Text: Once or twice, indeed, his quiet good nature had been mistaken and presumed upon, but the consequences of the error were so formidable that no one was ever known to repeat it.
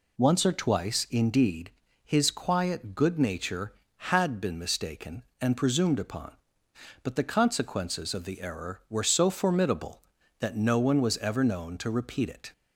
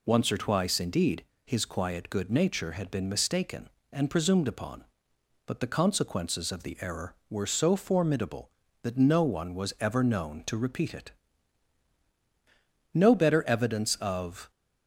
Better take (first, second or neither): first